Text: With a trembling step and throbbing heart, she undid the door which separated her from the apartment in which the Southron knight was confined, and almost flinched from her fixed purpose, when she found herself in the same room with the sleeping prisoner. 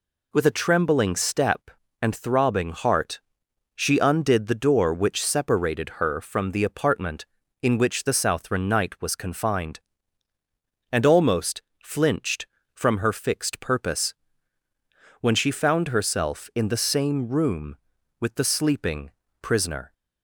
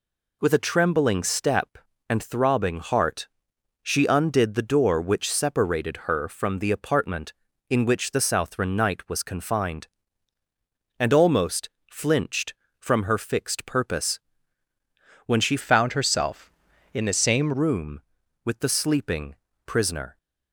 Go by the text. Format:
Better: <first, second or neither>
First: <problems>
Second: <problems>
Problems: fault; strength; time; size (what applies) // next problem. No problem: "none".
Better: first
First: pauses between "almost" and "flinched"; slight; at 11.6 s; 0.22 s long // pauses between "sleeping" and "prisoner"; slight; at 19.1 s; 0.30 s long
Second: pauses between "almost" and "flinched"; slight; at 11.6 s; 0.22 s long // changes voice from "found" to "same"; from 15.6 to 17.5 s; 1.9 s long // pauses between "sleeping" and "prisoner"; slight; at 19.3 s; 0.30 s long